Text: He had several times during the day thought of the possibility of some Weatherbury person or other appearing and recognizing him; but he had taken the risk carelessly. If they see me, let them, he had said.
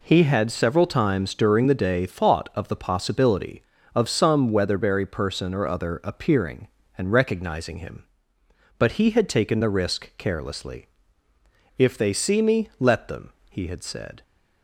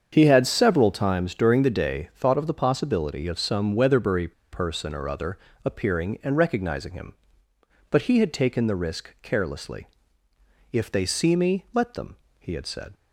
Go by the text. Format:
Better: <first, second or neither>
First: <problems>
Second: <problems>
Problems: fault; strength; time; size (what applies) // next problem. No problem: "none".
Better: first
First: none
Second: starts louder than the rest; strong; until 1.1 s; 7.5 dB // pauses between "Weatherbury" and "person"; slight; at 4.3 s; 0.20 s long // pauses between "other" and "appearing"; slight; at 5.3 s; 0.28 s long